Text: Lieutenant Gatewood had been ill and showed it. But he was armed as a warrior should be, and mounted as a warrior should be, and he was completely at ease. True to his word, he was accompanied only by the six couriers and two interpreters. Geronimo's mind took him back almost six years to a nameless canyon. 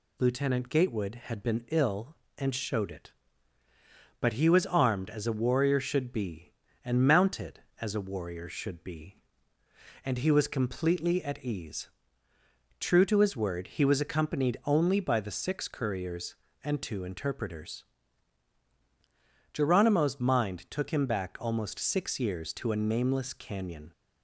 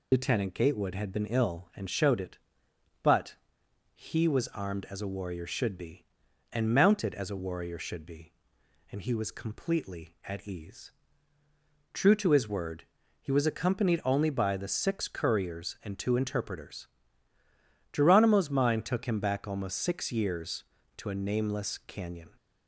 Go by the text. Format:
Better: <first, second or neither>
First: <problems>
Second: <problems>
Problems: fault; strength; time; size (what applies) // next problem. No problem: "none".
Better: first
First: none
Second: loses the start of "Lieutenant"; at 0.1 s; 50 ms // pauses between "But" and "he"; noticeable; at 3.3 s; 0.60 s long